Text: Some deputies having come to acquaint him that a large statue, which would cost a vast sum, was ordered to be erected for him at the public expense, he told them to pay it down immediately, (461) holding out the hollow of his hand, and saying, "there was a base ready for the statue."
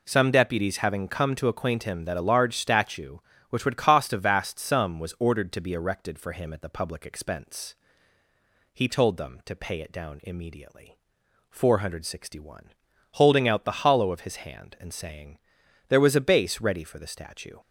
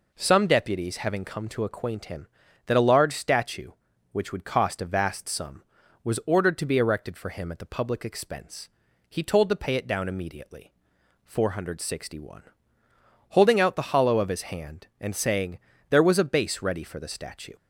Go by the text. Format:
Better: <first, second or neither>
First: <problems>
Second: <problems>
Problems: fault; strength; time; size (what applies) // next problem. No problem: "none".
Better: first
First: none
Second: skips "them"; at 9.4 s